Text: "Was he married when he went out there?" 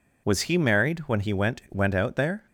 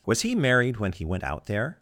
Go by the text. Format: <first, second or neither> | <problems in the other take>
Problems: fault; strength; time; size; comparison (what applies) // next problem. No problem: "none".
second | says "went" twice; at 1.6 s